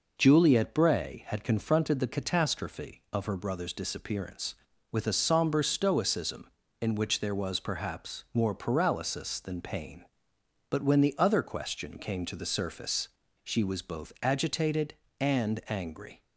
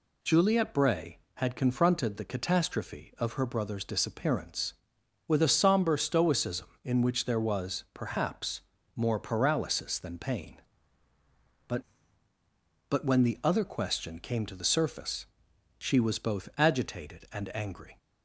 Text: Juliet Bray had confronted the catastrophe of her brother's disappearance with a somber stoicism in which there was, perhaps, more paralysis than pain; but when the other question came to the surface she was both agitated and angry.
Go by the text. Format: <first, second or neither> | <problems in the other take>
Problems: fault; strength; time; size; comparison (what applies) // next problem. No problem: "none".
first | says "but" twice; at 12.8 s // pauses between "surface" and "she"; noticeable; at 15.2 s; 0.54 s long; slight in the first